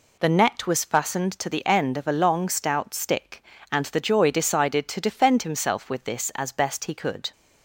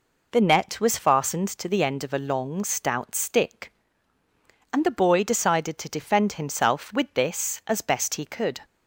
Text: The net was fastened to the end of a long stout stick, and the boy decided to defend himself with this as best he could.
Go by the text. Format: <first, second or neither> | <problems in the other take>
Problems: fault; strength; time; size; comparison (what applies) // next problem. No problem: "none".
second | says "joy" for "boy"; at 3.9 s